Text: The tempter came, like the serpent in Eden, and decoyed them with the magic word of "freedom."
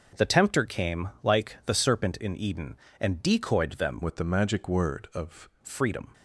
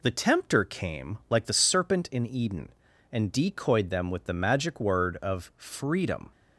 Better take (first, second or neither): second